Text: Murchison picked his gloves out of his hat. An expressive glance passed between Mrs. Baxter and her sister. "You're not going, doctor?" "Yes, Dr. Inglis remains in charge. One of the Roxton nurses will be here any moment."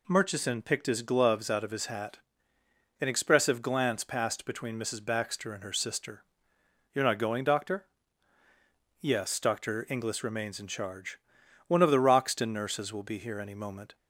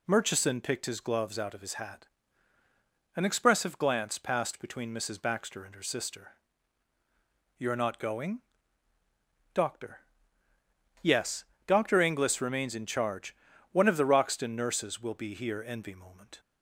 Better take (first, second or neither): first